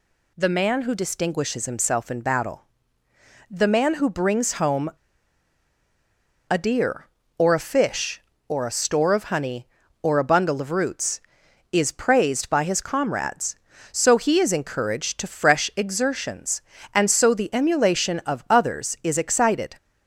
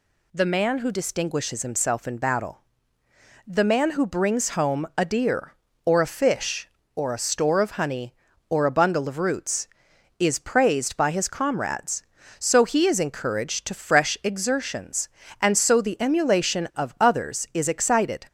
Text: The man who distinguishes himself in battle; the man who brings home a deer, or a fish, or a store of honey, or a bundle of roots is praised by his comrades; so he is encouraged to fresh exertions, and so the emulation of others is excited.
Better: second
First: pauses between "home" and "a"; strong; at 4.8 s; 1.5 s long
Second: none

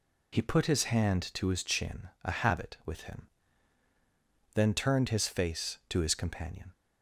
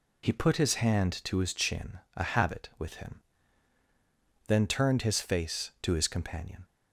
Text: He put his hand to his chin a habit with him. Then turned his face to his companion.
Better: neither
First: pauses between "chin" and "a"; slight; at 2.0 s; 0.16 s long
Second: pauses between "chin" and "a"; slight; at 1.9 s; 0.18 s long

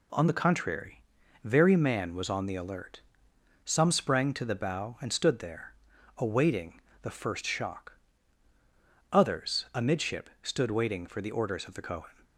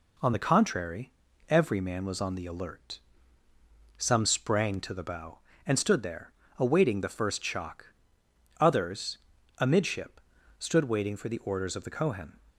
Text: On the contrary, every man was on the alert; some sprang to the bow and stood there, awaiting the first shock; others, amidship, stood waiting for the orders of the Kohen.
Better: second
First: says "very" for "every"; at 1.4 s // pauses between "awaiting" and "the"; slight; at 6.8 s; 0.22 s long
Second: none

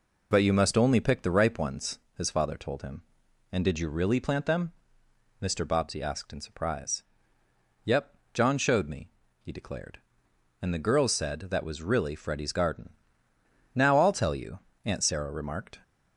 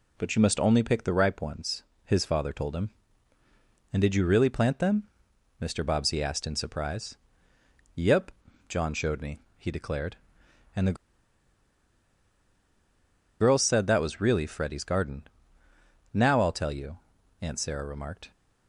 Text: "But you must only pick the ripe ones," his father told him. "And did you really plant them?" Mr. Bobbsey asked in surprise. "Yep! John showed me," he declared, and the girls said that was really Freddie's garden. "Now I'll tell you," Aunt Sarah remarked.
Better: first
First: none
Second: pauses between "the" and "girls"; strong; at 10.9 s; 2.4 s long

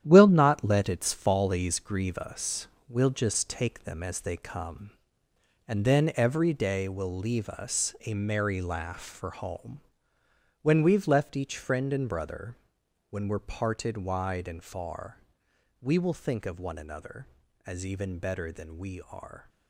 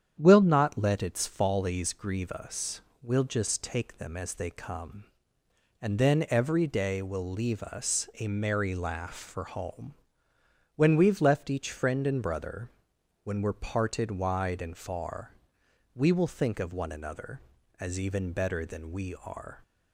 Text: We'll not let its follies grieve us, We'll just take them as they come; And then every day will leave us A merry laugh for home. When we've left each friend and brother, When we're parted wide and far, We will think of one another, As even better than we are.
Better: second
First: gets quieter; strong; throughout; 9 dB // starts louder than the rest; strong; until 1.0 s; 10.5 dB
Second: starts louder than the rest; strong; until 1.2 s; 8.5 dB

